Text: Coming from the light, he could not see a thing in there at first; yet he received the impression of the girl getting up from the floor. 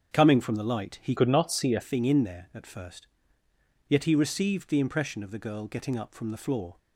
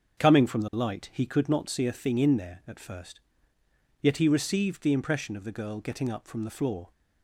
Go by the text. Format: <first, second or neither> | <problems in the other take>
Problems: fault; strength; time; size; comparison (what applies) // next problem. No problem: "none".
second | starts louder than the rest; until 1.1 s; 7 dB; also in the second // changes voice from "could" to "a"; from 1.1 to 1.8 s; 0.7 s long